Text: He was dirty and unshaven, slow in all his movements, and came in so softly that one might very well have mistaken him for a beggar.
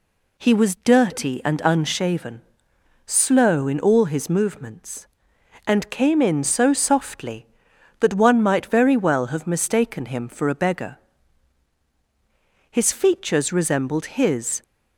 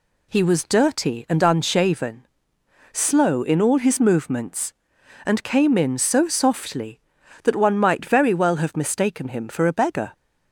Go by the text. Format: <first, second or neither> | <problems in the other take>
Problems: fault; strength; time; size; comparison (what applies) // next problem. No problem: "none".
second | goes on to say "His features resembled his"; strong; from 12.7 s on; 1.9 s long